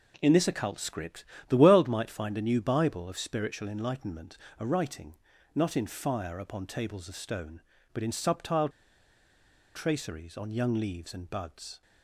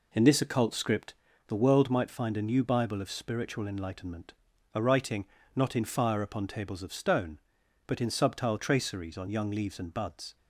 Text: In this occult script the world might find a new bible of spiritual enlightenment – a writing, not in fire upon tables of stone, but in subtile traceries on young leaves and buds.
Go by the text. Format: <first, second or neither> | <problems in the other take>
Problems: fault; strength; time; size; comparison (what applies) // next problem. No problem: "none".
second | pauses between "script" and "the"; slight; at 1.2 s; 0.24 s long; slight in the second // pauses between "subtile" and "traceries"; at 8.6 s; 1.0 s long